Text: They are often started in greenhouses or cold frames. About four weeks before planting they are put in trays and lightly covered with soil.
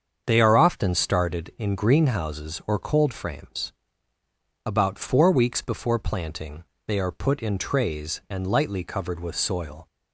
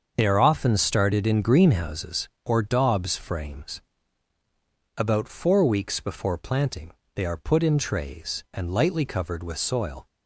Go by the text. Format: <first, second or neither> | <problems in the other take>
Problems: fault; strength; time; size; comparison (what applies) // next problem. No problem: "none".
first | starts louder than the rest; until 1.1 s; 6.5 dB; strong in the first // says "daubs" for "cold"; at 2.6 s // pauses between "planting" and "they"; slight; at 6.9 s; 0.22 s long; slight in the first